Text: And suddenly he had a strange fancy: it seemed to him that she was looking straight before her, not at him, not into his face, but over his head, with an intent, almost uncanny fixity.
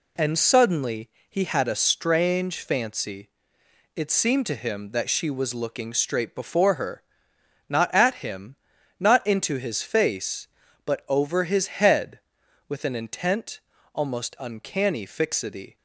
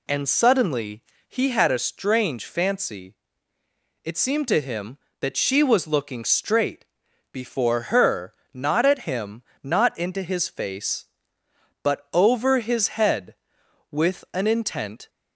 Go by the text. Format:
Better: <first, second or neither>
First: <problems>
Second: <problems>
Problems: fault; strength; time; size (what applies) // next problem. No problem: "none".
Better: first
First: pauses between "suddenly" and "he"; slight; at 1.0 s; 0.20 s long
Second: pauses between "suddenly" and "he"; slight; at 1.0 s; 0.26 s long // pauses between "straight" and "before"; noticeable; at 6.8 s; 0.48 s long // stops before "almost uncanny fixity"; at 15.0 s